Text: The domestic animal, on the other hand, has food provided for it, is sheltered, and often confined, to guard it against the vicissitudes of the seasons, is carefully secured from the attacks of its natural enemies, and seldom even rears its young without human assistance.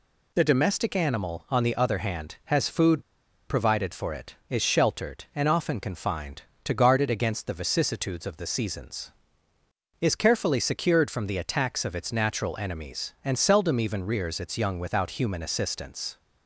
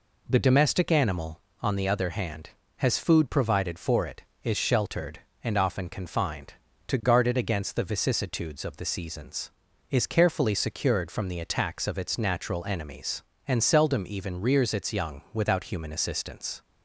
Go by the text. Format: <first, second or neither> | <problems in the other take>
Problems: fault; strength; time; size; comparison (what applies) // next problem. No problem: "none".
second | pauses between "food" and "provided"; at 3.0 s; 0.45 s long